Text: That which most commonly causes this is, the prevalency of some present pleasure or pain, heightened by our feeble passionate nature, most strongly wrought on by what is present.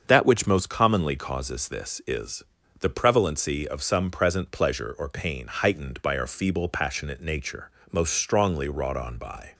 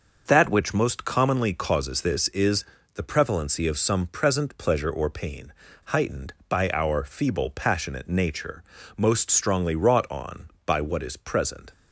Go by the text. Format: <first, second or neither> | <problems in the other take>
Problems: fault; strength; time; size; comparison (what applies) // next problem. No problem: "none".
second | starts louder than the rest; until 1.0 s; 7 dB; noticeable in the second // stops before "what is present"; at 9.5 s